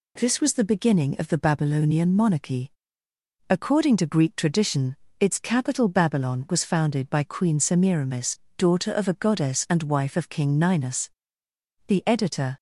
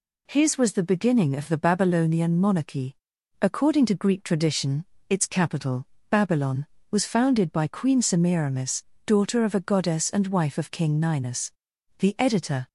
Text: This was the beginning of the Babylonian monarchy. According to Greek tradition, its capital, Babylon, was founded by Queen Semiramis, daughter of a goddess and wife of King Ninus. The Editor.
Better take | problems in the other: first | says "His" for "This"; at 0.2 s

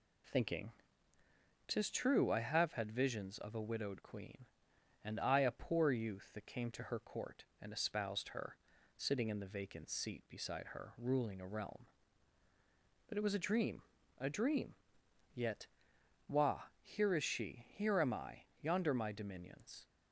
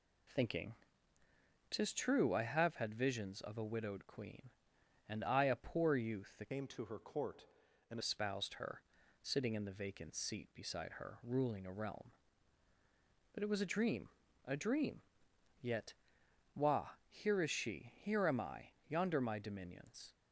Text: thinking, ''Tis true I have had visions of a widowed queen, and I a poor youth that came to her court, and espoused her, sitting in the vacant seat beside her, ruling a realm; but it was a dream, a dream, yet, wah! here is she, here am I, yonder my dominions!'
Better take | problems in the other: first | changes voice from "came" to "and"; from 6.5 to 7.9 s; 1.4 s long

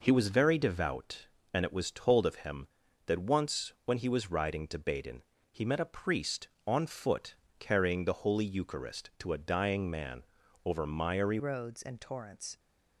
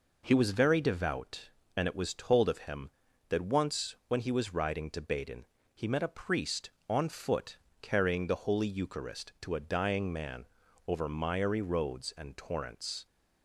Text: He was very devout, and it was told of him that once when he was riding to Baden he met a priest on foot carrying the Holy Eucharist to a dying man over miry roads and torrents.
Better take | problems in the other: second | pauses between "Baden" and "he"; slight; at 5.2 s; 0.30 s long; slight in the second // pauses between "foot" and "carrying"; slight; at 7.3 s; 0.24 s long; slight in the second // pauses between "man" and "over"; at 10.2 s; 0.42 s long; also in the second // changes voice at "roads"; from 11.3 s on; 1.2 s long

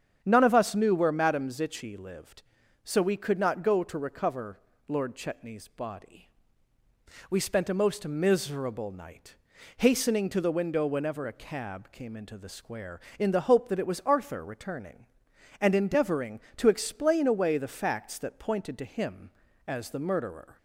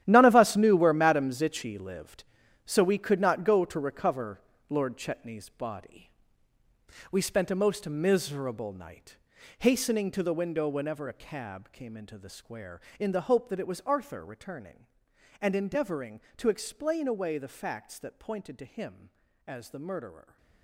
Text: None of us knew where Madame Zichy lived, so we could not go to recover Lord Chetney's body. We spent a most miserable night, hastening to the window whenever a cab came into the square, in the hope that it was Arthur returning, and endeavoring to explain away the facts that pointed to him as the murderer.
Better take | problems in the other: first | gets quieter; strong; throughout; 13.5 dB // starts louder than the rest; strong; until 1.0 s; 11 dB; strong in the first // pauses between "recover" and "Lord"; slight; at 4.4 s; 0.28 s long; slight in the first

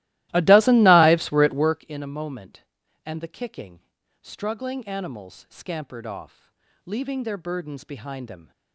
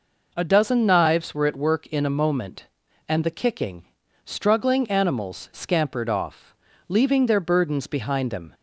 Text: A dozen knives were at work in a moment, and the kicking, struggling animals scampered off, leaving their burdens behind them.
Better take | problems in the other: second | starts louder than the rest; strong; until 1.9 s; 17 dB

